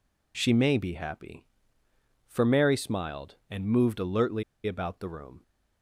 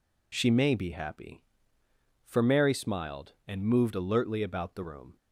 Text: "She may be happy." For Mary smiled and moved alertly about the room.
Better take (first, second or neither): second